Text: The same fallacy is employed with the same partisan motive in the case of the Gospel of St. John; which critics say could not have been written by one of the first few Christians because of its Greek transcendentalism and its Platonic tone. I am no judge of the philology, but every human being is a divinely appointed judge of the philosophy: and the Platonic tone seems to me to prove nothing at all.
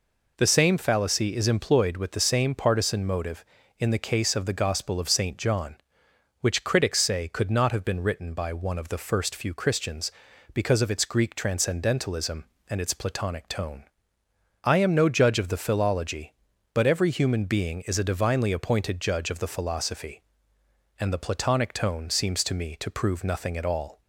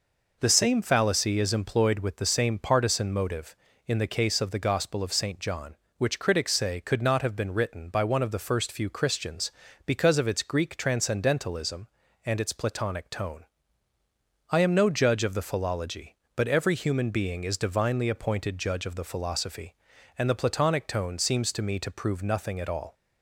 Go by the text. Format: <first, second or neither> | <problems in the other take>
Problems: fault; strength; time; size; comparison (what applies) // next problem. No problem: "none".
first | skips "a"; at 17.5 s